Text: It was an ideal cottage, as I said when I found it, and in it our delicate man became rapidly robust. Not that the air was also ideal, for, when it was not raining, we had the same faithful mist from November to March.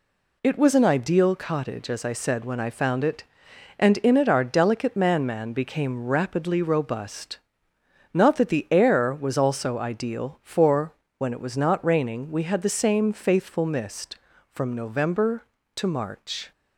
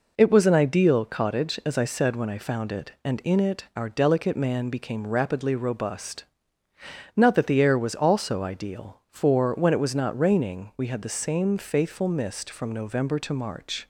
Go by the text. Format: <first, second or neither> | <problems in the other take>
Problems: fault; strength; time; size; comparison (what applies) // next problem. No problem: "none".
second | says "man" twice; at 5.2 s